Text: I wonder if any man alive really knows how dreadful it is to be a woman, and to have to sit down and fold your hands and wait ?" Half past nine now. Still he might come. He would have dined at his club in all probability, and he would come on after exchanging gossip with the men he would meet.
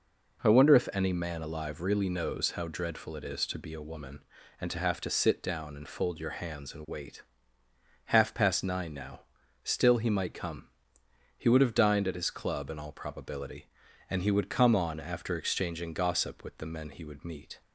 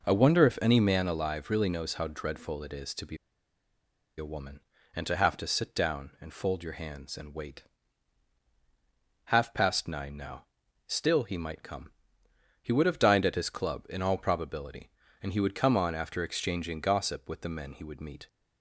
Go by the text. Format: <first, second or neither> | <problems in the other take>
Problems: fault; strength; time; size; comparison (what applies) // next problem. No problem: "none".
first | pauses between "be" and "a"; at 3.1 s; 1.0 s long